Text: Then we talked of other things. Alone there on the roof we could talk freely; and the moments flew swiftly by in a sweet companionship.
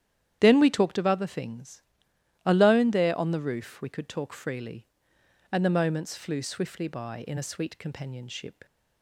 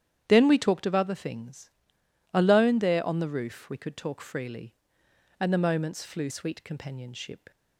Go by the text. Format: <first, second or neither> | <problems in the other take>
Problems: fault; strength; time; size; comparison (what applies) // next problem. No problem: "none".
first | starts louder than the rest; strong; until 1.2 s; 10 dB; strong in the first // skips "swiftly by in a"; at 6.2 s